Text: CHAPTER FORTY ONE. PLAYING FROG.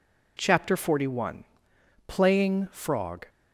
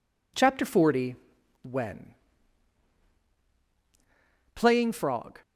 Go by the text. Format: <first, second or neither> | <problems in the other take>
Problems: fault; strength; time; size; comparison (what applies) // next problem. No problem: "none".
first | says "When" for "ONE"; at 1.6 s